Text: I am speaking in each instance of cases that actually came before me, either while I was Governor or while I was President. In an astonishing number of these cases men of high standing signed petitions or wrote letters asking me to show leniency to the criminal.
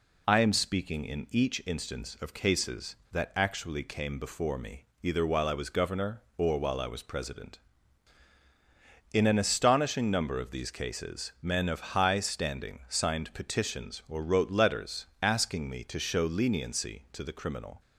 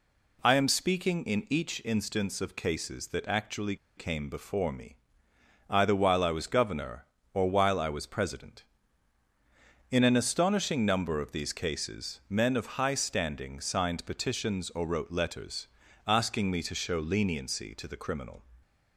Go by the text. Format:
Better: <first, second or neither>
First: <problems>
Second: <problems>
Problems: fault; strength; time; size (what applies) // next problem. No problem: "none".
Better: first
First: pauses between "letters" and "asking"; slight; at 15.0 s; 0.16 s long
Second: pauses between "actually" and "came"; slight; at 3.7 s; 0.21 s long // pauses between "letters" and "asking"; at 15.6 s; 0.38 s long